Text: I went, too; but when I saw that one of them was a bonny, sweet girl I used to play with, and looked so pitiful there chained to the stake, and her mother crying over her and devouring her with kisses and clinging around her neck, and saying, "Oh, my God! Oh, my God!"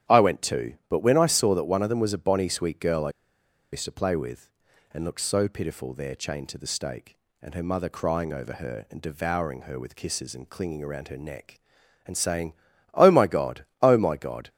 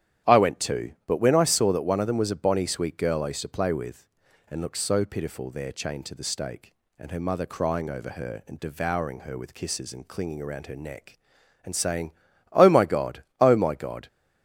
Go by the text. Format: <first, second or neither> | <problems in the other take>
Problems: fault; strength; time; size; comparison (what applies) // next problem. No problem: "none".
second | starts louder than the rest; strong; until 1.2 s; 10.5 dB; strong in the second // pauses between "I" and "used"; noticeable; at 3.0 s; 0.62 s long